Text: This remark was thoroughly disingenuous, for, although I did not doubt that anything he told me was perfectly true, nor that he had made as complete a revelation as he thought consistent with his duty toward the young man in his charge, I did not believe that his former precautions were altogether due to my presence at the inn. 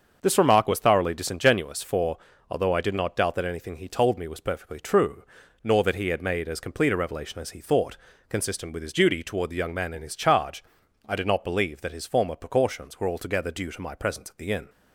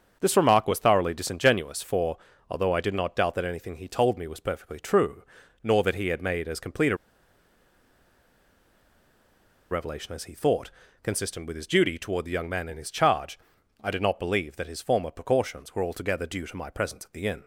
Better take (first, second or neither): first